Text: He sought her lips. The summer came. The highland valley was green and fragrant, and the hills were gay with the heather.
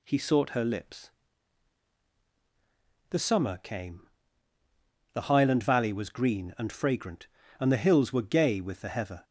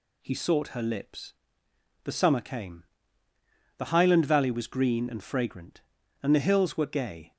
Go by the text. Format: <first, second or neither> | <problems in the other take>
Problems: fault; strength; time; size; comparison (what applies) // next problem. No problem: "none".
first | stops before "with the heather"; at 7.3 s